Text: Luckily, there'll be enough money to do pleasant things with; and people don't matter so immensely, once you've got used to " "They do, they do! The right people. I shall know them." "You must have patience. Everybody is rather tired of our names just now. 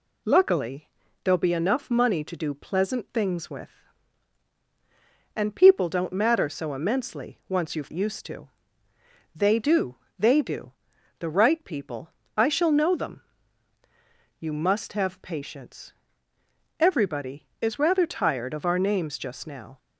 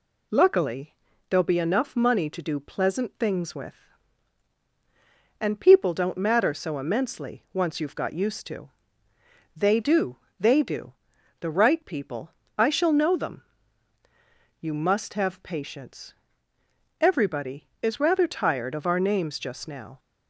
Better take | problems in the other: second | skips "got"; at 7.9 s

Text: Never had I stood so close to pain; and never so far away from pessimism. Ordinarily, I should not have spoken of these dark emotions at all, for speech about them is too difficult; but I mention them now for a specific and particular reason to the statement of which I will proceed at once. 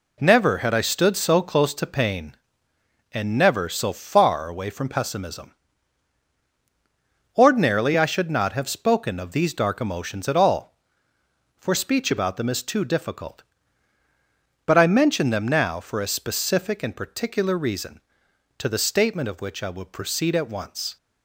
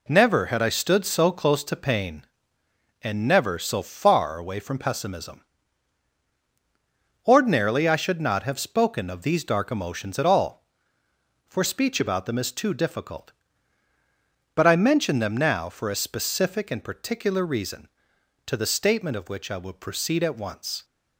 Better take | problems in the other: neither | none

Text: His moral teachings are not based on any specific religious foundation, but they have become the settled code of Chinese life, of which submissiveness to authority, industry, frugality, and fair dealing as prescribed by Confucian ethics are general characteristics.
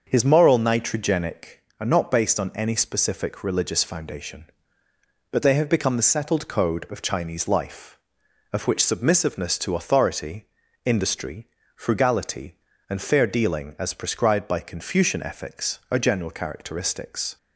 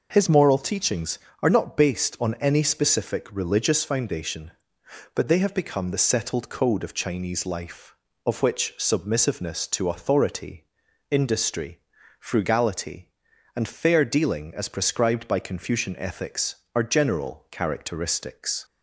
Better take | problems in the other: second | starts louder than the rest; until 1.1 s; 6 dB // says "nitrogenic" for "teachings"; at 0.5 s

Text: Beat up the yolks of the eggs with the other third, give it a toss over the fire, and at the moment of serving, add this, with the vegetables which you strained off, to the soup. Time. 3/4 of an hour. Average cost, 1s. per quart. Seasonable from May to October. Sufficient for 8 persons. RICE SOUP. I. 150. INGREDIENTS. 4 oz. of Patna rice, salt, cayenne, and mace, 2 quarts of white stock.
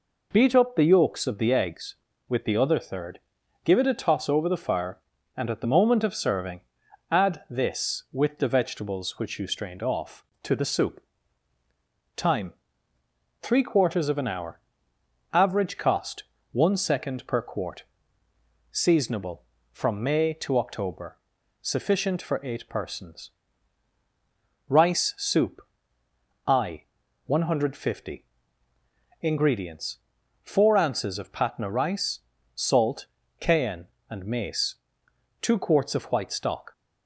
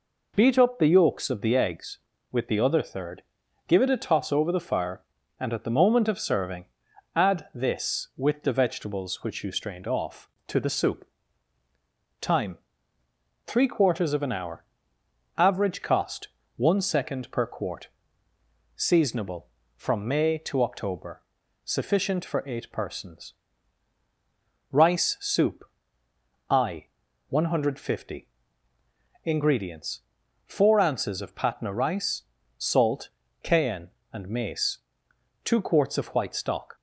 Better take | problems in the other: neither | none

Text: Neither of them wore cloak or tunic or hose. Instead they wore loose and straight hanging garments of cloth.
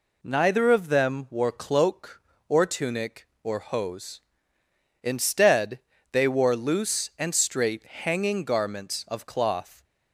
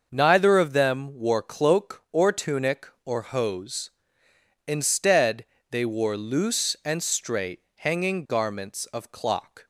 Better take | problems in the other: first | starts louder than the rest; until 1.1 s; 6.5 dB // pauses between "Instead" and "they"; slight; at 5.4 s; 0.24 s long; slight in the first // says "clock" for "cloth"; at 9.1 s

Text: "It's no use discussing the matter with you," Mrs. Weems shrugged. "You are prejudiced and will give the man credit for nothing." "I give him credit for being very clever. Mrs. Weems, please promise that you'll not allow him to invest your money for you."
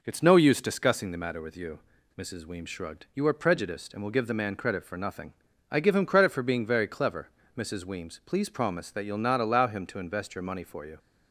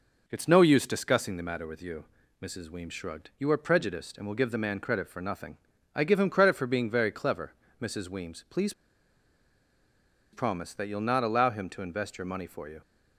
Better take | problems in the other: first | pauses between "please" and "promise"; strong; at 8.7 s; 1.6 s long

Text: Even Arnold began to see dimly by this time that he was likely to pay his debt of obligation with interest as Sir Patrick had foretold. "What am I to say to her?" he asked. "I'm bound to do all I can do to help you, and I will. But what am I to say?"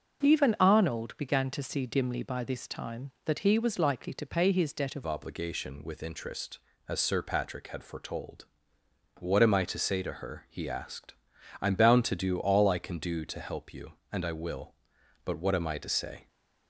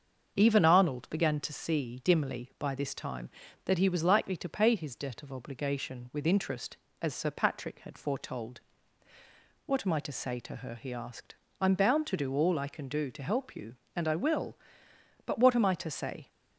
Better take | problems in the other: second | starts louder than the rest; noticeable; until 1.2 s; 6 dB; also in the second // changes voice at "obligation"; from 5.0 s on; 11.2 s long

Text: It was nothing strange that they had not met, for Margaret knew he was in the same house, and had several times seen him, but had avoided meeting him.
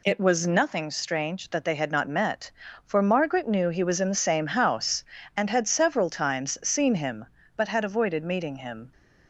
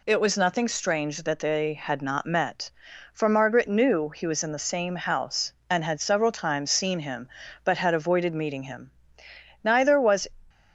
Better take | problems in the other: first | goes on to say "Neither was"; noticeable; from 9.6 s on; 0.64 s long

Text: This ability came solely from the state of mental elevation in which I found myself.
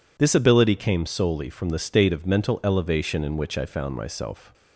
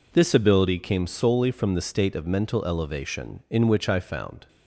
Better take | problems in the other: first | stops before "myself"; at 4.4 s

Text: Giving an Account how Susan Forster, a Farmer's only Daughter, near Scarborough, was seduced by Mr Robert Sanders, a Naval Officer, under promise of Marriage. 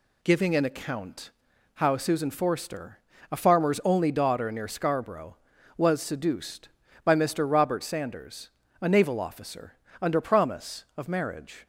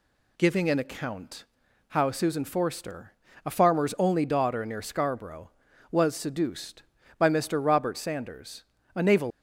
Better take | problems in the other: first | pauses between "Account" and "how"; at 1.4 s; 0.44 s long; also in the first // stops before "Officer under promise of Marriage"; at 9.3 s

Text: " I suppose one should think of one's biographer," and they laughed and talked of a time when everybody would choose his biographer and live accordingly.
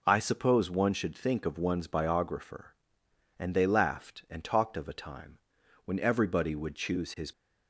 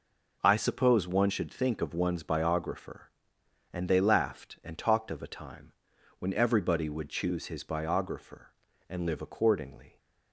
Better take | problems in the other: second | pauses between "time" and "when"; noticeable; at 5.3 s; 0.48 s long; noticeable in the second // stops before "biographer and live accordingly"; at 7.3 s

